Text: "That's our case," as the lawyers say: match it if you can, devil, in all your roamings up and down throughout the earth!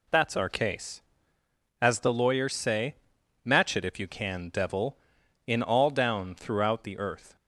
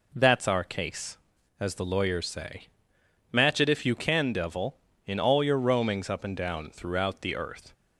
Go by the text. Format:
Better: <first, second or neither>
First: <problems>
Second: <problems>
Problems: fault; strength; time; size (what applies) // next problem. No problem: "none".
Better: second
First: skips "your roamings up and"; at 5.8 s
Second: none